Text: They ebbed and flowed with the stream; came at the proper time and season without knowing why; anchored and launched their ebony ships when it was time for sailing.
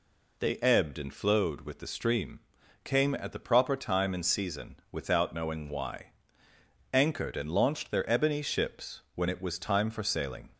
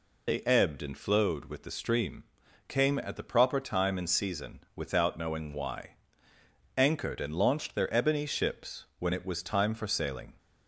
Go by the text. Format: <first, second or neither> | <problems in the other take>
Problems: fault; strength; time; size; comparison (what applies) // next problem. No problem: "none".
first | loses the start of "They"; at 0.2 s; 50 ms // pauses between "season" and "without"; slight; at 4.5 s; 0.16 s long; slight in the first